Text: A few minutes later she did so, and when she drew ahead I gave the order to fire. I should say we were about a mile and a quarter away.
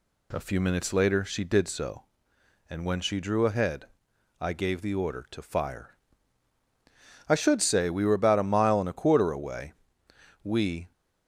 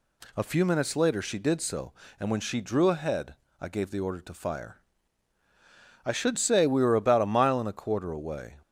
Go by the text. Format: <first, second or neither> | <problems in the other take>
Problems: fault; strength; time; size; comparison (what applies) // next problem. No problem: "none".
second | pauses between "ahead" and "I"; noticeable; at 3.8 s; 0.54 s long; slight in the second // goes on to say "We"; slight; from 10.4 s on; 0.48 s long